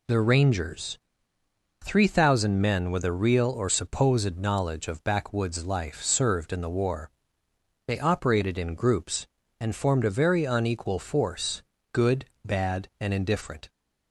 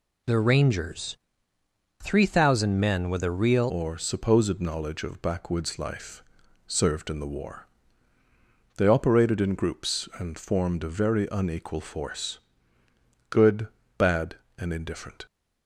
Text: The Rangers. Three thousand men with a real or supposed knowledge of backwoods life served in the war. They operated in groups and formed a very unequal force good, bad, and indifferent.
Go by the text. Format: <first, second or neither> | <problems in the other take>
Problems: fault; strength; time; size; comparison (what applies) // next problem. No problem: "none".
first | changes voice at "or"; from 3.6 s on; 11.6 s long // pauses between "life" and "served"; at 6.2 s; 0.42 s long // pauses between "force" and "good"; noticeable; at 12.3 s; 0.90 s long; slight in the first